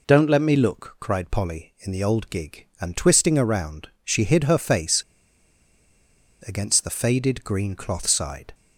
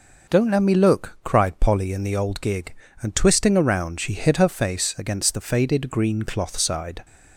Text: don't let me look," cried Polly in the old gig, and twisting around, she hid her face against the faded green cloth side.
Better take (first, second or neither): second